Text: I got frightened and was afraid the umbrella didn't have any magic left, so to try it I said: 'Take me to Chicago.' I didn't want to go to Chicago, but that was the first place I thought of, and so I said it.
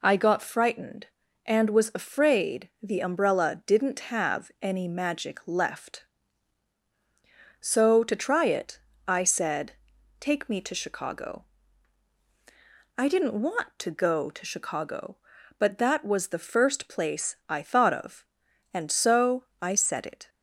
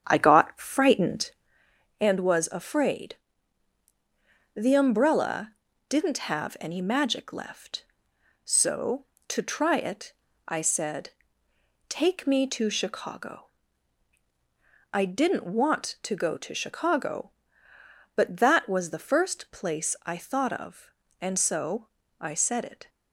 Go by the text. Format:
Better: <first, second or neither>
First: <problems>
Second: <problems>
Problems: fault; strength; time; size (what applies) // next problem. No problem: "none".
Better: first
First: pauses between "it" and "I"; slight; at 8.7 s; 0.28 s long // pauses between "so" and "I"; slight; at 19.4 s; 0.18 s long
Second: starts louder than the rest; strong; until 1.5 s; 8.5 dB // pauses between "afraid" and "the"; strong; at 3.1 s; 1.4 s long // pauses between "umbrella" and "didn't"; slight; at 5.5 s; 0.36 s long // pauses between "it" and "I"; slight; at 10.1 s; 0.34 s long // pauses between "so" and "I"; slight; at 21.8 s; 0.34 s long